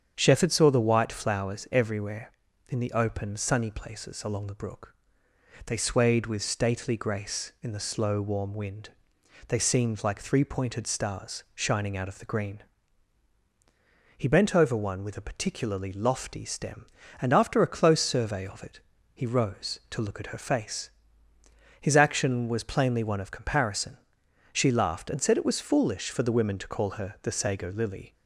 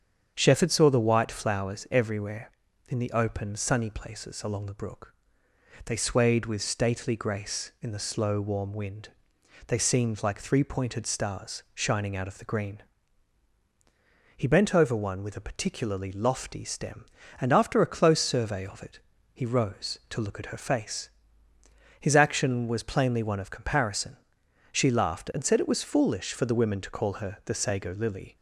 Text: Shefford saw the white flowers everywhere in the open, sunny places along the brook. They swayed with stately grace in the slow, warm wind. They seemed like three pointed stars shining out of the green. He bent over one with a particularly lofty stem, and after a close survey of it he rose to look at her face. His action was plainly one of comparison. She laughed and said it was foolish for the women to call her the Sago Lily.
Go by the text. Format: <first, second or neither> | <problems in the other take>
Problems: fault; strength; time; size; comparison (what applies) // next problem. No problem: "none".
neither | starts louder than the rest; strong; the same in both // pauses between "it" and "he"; slight; the same in both